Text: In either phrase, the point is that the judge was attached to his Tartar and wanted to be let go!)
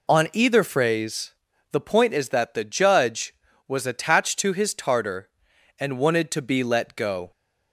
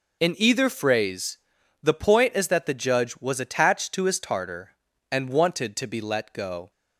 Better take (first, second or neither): second